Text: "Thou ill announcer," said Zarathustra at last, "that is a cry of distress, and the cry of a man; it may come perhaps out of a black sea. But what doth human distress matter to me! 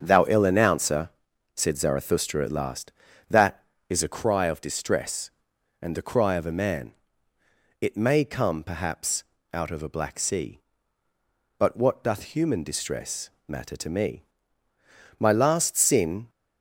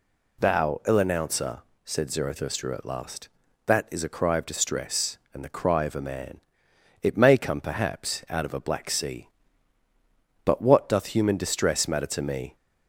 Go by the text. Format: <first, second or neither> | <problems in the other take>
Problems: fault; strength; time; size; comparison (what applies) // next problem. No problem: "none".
second | starts louder than the rest; until 1.0 s; 7 dB // pauses between "perhaps" and "out"; slight; at 9.2 s; 0.30 s long // pauses between "distress" and "matter"; slight; at 13.2 s; 0.18 s long // goes on to say "My last sin"; noticeable; from 15.1 s on; 1.1 s long